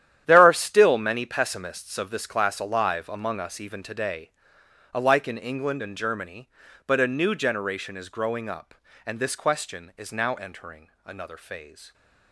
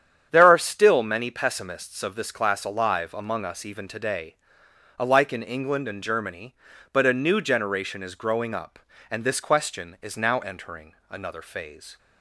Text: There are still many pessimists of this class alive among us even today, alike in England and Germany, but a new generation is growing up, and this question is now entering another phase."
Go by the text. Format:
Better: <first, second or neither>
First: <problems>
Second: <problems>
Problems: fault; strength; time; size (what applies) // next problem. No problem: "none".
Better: second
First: gets quieter; strong; throughout; 13 dB // starts louder than the rest; strong; until 1.2 s; 10.5 dB // pauses between "entering" and "another"; slight; at 10.8 s; 0.16 s long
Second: starts louder than the rest; strong; until 1.3 s; 8.5 dB // pauses between "entering" and "another"; slight; at 10.9 s; 0.16 s long